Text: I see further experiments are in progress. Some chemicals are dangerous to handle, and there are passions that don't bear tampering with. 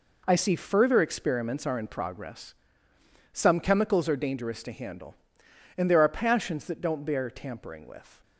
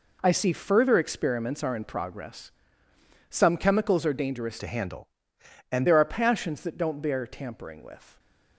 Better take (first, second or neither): first